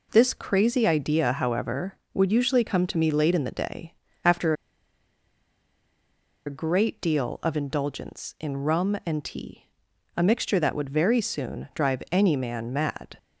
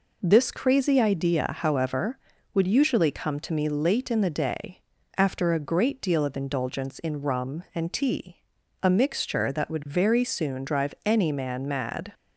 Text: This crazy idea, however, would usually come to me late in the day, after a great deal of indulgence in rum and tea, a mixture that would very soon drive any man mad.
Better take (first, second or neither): second